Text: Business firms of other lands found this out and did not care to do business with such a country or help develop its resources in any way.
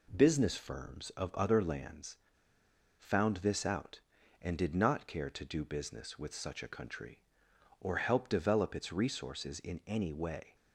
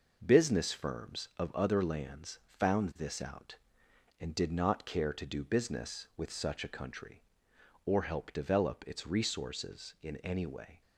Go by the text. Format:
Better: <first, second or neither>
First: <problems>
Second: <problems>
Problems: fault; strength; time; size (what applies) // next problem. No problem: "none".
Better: second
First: pauses between "lands" and "found"; noticeable; at 2.1 s; 0.80 s long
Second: none